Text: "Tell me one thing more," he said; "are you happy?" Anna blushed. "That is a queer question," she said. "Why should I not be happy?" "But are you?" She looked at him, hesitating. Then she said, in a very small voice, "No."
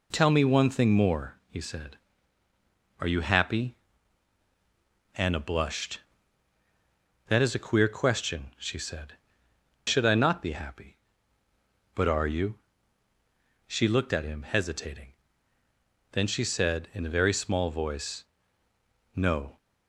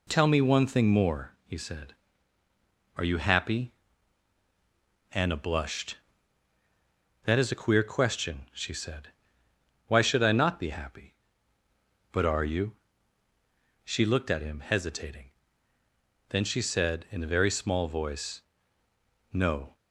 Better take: second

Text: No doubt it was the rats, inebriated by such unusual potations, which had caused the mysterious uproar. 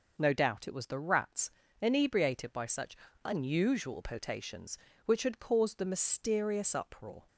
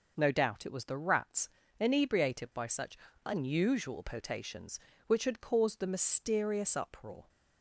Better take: neither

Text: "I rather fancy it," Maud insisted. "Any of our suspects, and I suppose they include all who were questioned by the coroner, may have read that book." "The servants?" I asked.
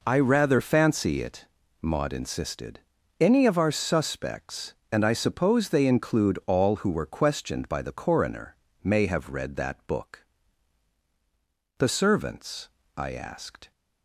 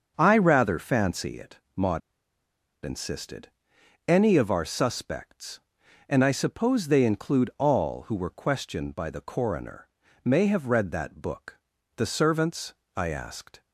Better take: first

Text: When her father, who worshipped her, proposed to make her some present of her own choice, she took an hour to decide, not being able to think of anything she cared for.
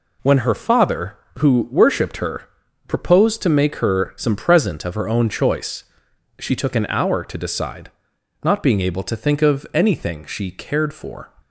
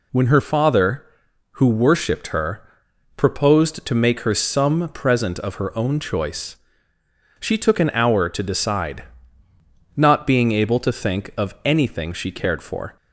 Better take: neither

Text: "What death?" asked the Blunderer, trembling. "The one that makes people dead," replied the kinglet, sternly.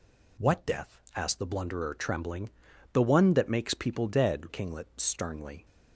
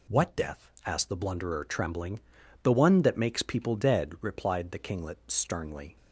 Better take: second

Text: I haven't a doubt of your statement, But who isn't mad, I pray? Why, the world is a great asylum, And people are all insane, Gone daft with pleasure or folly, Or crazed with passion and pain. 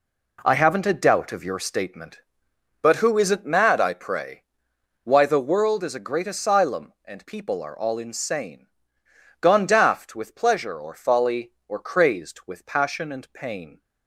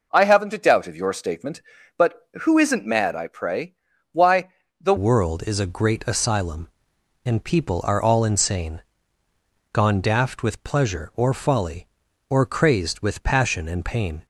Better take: first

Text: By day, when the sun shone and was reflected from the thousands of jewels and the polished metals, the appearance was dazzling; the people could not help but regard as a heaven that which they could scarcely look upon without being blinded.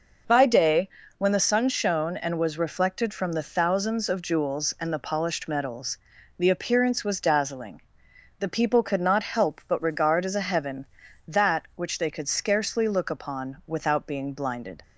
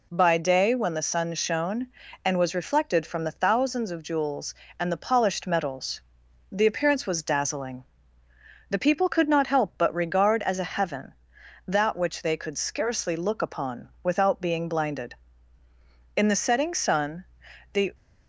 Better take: first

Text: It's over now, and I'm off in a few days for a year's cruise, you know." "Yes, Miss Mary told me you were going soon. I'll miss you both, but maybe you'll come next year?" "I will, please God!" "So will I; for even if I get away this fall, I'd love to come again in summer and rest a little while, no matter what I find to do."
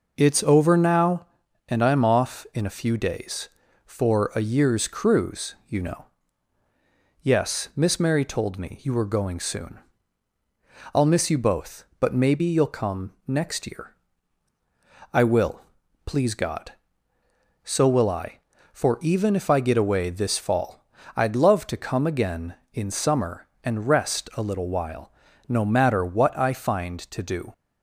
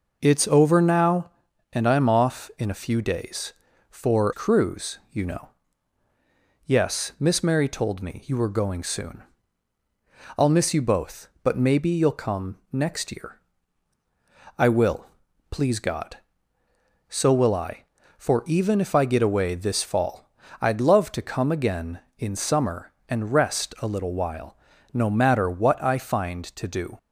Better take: first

